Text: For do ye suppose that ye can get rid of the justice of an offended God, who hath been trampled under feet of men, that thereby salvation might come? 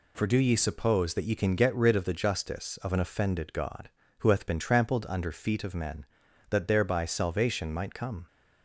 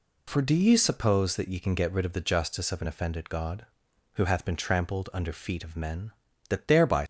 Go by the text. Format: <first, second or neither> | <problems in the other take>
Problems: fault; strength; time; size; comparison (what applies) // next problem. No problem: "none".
first | stops before "salvation might come"; at 7.0 s